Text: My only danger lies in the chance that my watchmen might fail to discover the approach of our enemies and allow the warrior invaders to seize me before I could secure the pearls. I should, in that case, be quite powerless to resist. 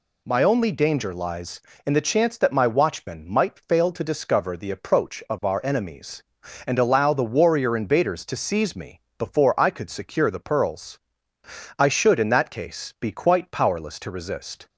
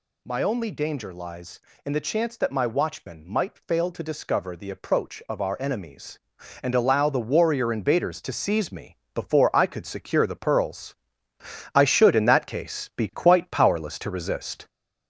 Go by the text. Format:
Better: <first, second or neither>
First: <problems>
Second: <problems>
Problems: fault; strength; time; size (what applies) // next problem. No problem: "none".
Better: first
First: pauses between "me" and "before"; slight; at 9.0 s; 0.18 s long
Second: gets louder; noticeable; throughout; 4.5 dB // pauses between "me" and "before"; slight; at 8.9 s; 0.18 s long